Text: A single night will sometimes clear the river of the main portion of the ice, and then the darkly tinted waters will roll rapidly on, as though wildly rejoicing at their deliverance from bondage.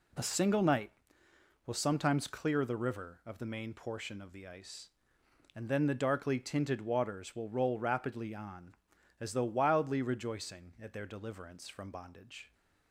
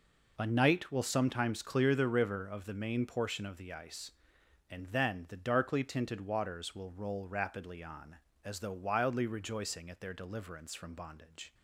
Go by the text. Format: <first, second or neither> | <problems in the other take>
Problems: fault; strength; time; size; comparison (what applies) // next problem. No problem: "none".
first | skips "single"; at 0.4 s